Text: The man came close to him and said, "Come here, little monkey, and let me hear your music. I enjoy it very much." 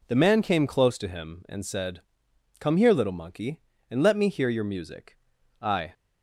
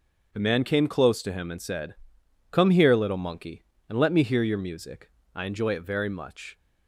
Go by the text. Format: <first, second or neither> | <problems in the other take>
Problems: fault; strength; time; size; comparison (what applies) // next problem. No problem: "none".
second | stops before "enjoy it very much"; at 5.9 s